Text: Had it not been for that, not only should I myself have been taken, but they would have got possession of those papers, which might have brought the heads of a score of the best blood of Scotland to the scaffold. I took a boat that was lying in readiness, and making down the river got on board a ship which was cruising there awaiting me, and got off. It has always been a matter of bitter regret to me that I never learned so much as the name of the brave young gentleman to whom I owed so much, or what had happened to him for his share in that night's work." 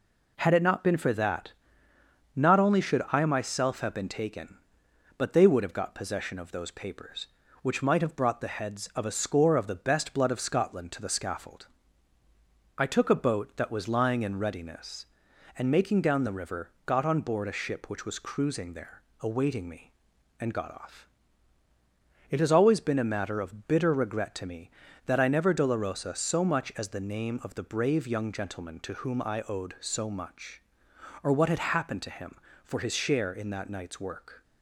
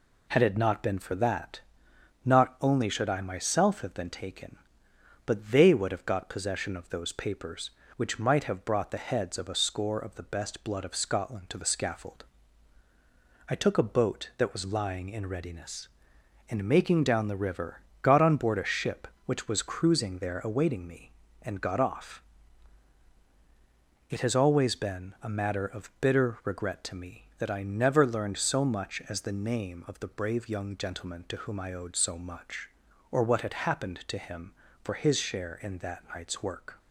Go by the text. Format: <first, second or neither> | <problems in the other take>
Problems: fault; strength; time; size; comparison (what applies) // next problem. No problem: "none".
second | pauses between "river" and "got"; slight; at 16.7 s; 0.16 s long; slight in the second // pauses between "there" and "awaiting"; slight; at 19.0 s; 0.20 s long // says "dolorosa" for "learned"; at 25.5 s